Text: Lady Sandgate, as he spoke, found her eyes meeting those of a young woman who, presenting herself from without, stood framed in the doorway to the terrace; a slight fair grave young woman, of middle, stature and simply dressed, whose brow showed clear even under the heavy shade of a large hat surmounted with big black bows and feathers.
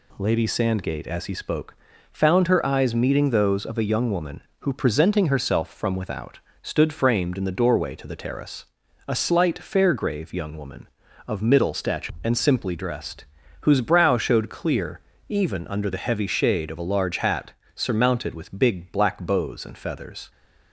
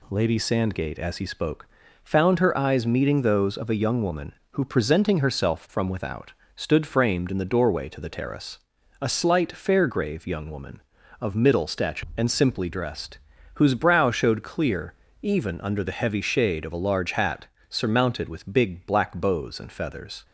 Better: neither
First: pauses between "clear" and "even"; slight; at 14.9 s; 0.30 s long // pauses between "hat" and "surmounted"; slight; at 17.5 s; 0.24 s long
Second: pauses between "clear" and "even"; slight; at 14.9 s; 0.30 s long // pauses between "hat" and "surmounted"; slight; at 17.4 s; 0.24 s long

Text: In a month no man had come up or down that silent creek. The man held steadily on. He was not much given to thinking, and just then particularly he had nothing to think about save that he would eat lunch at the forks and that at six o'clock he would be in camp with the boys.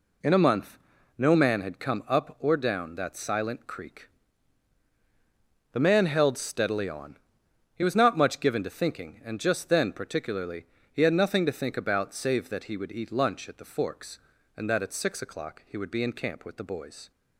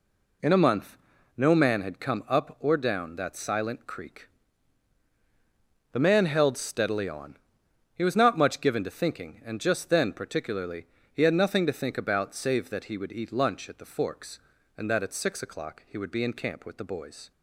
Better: neither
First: pauses between "month" and "no"; at 0.7 s; 0.40 s long // pauses between "particularly" and "he"; slight; at 10.6 s; 0.28 s long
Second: pauses between "month" and "no"; at 0.9 s; 0.40 s long // pauses between "particularly" and "he"; slight; at 10.8 s; 0.28 s long

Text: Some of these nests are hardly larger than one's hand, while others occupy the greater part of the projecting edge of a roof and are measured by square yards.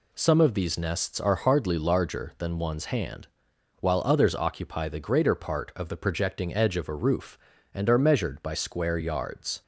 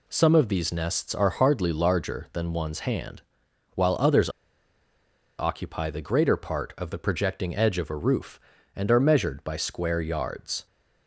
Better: first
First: none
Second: pauses between "others" and "occupy"; at 4.2 s; 1.1 s long

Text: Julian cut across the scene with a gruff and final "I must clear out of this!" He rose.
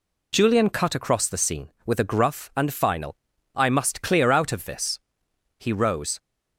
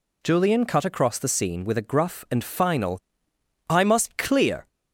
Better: first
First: pauses between "final" and "I"; at 3.1 s; 0.40 s long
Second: pauses between "final" and "I"; noticeable; at 2.9 s; 0.68 s long // stops before "out of this He rose"; at 4.6 s

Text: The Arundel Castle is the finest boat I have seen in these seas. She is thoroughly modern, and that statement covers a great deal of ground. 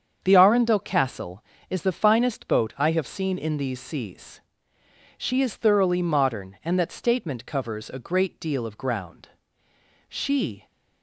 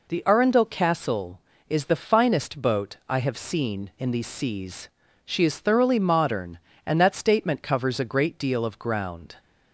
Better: second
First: starts louder than the rest; strong; until 1.2 s; 7.5 dB // goes on to say "She"; from 10.0 s on; 0.58 s long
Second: none

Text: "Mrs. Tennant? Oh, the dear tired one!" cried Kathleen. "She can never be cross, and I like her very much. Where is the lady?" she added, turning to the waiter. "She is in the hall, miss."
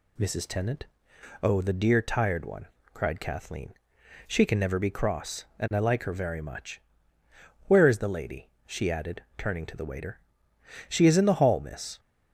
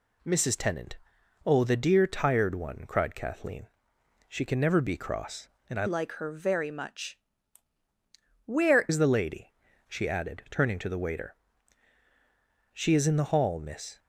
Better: first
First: none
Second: changes voice from "like" to "Where"; from 5.8 to 8.8 s; 3.0 s long

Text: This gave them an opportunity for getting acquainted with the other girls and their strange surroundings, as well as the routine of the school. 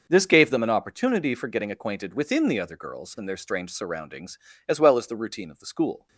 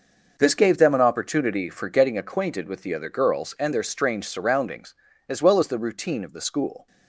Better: second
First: starts louder than the rest; noticeable; until 1.1 s; 6 dB // says "within" for "with"; at 2.1 s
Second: none

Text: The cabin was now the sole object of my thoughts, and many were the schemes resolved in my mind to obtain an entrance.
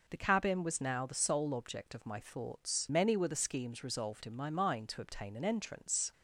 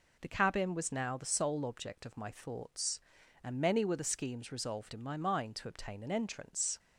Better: second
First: skips "and"; at 2.9 s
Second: none

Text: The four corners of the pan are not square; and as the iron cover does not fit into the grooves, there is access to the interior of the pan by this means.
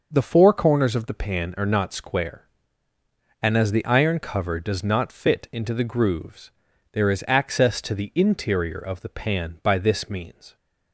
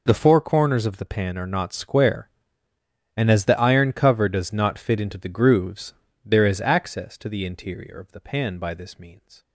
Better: neither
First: none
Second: none

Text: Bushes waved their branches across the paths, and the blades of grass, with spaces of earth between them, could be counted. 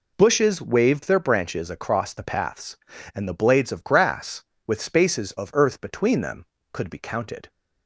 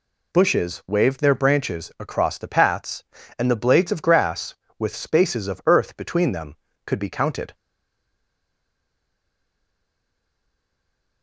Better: first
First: none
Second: stays silent after the last word; strong; from 7.5 s on; 3.7 s long

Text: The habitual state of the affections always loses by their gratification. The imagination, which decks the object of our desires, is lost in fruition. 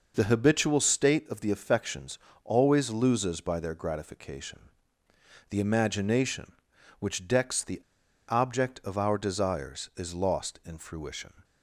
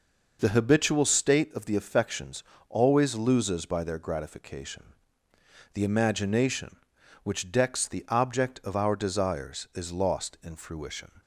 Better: second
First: pauses between "affections" and "always"; slight; at 2.1 s; 0.28 s long // pauses between "the" and "object"; noticeable; at 7.8 s; 0.46 s long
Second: pauses between "affections" and "always"; slight; at 2.4 s; 0.28 s long

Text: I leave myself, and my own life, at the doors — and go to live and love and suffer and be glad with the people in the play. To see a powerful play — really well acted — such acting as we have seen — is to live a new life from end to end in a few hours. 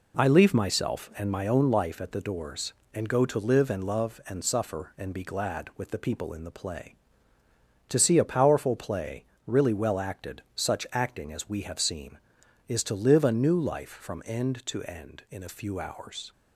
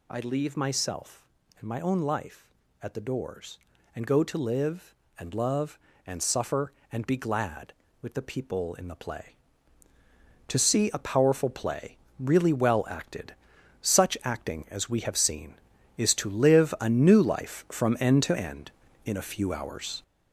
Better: first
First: none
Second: gets louder; throughout; 6.5 dB

